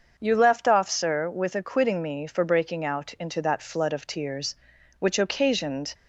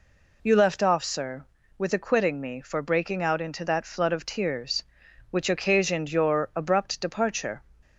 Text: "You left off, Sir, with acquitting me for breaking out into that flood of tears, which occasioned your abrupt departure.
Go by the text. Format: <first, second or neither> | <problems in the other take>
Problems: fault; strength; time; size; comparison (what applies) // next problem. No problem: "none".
second | starts louder than the rest; until 1.1 s; 6.5 dB // stops before "your abrupt departure"; at 5.9 s